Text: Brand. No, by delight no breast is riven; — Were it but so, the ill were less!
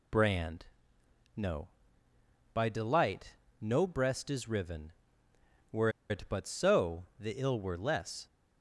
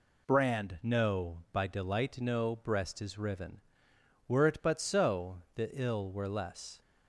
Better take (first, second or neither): second